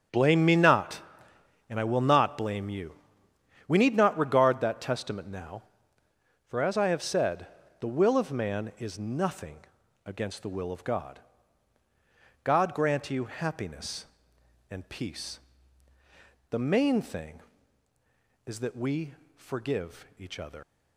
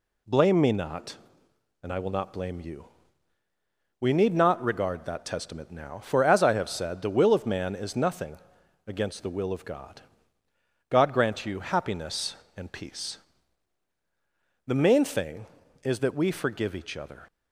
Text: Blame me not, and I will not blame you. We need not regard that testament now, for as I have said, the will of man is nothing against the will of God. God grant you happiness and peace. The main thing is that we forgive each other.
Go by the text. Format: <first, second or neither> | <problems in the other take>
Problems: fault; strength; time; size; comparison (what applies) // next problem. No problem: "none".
second | starts louder than the rest; strong; until 1.7 s; 8 dB // pauses between "nothing" and "against"; noticeable; at 9.5 s; 0.48 s long; noticeable in the second // pauses between "we" and "forgive"; slight; at 19.1 s; 0.22 s long // leaves "other" unfinished; at 20.6 s; 80 ms